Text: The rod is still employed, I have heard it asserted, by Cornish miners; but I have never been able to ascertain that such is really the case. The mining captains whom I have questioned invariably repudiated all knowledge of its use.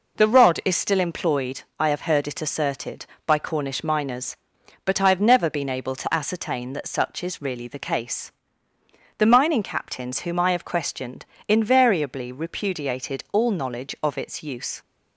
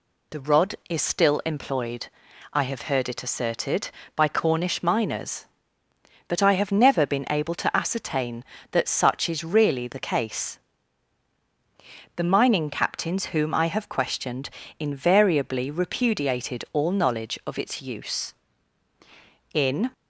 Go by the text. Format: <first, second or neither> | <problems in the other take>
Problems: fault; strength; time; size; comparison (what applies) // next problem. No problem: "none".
first | pauses between "questioned" and "invariably"; slight; at 14.5 s; 0.26 s long; slight in the first // goes on to say "In"; slight; from 19.5 s on; 0.34 s long